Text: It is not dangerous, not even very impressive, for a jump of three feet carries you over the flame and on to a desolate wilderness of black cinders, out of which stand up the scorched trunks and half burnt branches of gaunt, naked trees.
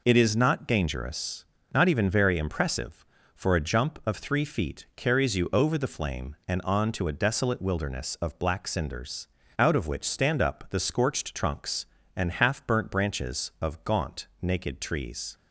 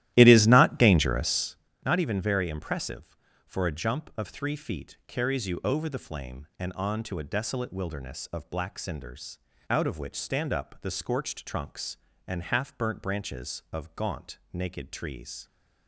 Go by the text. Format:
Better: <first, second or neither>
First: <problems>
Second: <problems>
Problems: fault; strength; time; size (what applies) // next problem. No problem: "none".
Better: first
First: none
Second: starts louder than the rest; strong; until 1.7 s; 14 dB